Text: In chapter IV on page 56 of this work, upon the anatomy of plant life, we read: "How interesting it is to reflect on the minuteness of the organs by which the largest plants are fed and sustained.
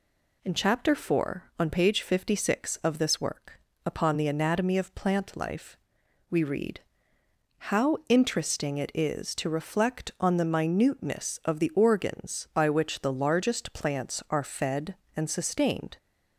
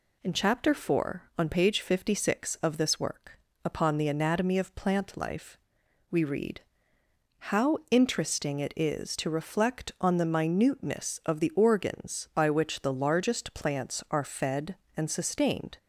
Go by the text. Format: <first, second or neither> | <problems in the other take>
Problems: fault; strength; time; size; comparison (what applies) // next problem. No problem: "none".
neither | none